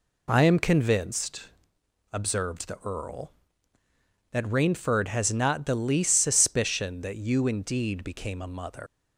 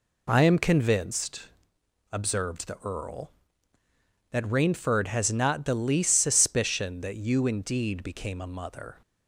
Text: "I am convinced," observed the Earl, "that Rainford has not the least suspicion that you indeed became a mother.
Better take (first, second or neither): second